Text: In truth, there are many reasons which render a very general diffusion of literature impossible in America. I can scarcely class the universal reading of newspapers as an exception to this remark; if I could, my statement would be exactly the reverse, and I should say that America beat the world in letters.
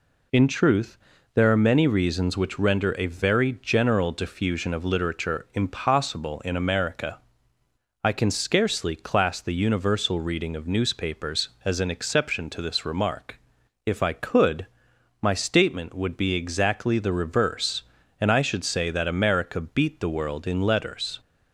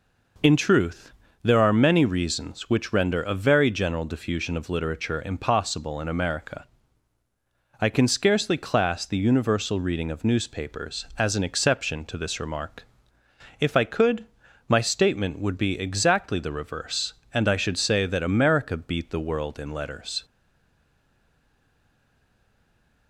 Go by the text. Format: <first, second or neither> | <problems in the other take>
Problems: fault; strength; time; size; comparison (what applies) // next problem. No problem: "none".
first | stays silent after the last word; strong; from 20.2 s on; 2.8 s long